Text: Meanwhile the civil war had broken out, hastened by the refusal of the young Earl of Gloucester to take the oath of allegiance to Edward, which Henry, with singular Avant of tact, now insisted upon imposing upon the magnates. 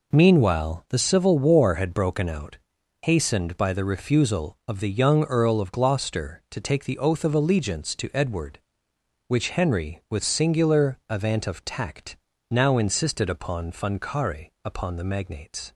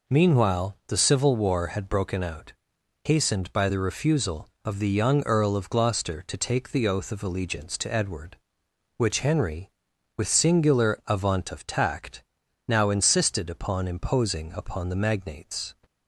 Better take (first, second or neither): second